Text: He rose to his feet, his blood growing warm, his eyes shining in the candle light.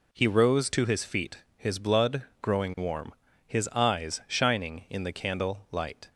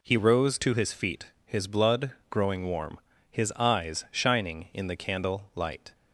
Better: neither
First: pauses between "blood" and "growing"; slight; at 2.2 s; 0.18 s long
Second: pauses between "blood" and "growing"; slight; at 2.1 s; 0.18 s long

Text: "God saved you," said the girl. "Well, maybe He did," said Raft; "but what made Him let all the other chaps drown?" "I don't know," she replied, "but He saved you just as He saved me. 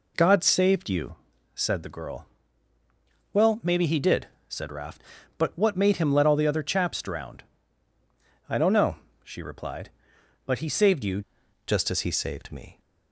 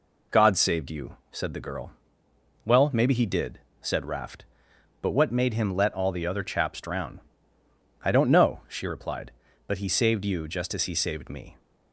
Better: second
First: changes voice at "just"; from 11.6 s on; 1.1 s long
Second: none

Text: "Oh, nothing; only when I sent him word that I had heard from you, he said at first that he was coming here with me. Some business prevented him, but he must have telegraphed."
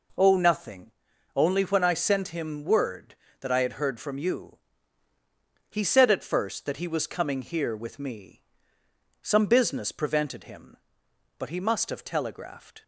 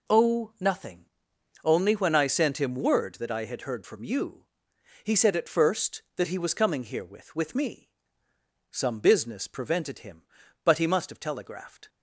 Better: first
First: none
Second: says "with" twice; at 7.3 s

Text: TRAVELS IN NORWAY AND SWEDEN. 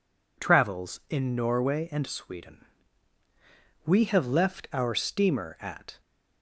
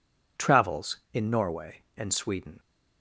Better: second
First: goes on to say "WE have left our steamer at"; strong; from 3.8 s on; 2.1 s long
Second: none

